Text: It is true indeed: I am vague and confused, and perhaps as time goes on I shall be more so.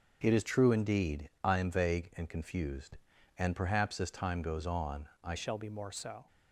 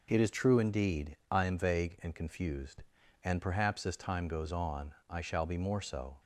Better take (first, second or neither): second